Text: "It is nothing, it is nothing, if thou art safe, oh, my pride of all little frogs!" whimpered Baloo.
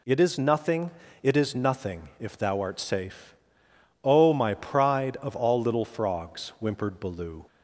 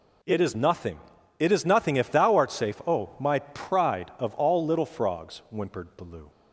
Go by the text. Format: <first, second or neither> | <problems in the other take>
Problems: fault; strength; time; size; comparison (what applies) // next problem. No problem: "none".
neither | none